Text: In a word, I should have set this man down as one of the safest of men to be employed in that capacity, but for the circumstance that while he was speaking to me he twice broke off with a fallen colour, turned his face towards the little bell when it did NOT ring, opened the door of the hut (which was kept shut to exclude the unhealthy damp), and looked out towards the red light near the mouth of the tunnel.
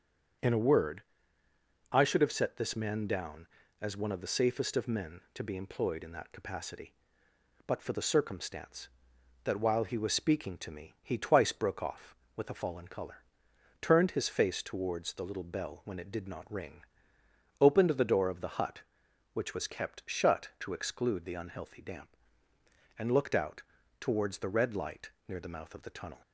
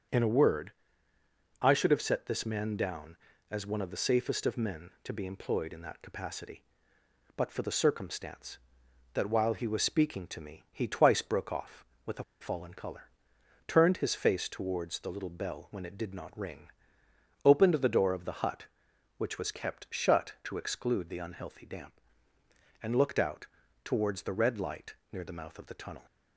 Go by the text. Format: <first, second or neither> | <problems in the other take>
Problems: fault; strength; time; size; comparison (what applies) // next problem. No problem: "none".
first | starts louder than the rest; strong; until 2.0 s; 7 dB; strong in the first // pauses between "a" and "fallen"; slight; at 12.2 s; 0.17 s long // pauses between "out" and "towards"; at 23.4 s; 0.38 s long; also in the first // pauses between "light" and "near"; slight; at 24.9 s; 0.16 s long; slight in the first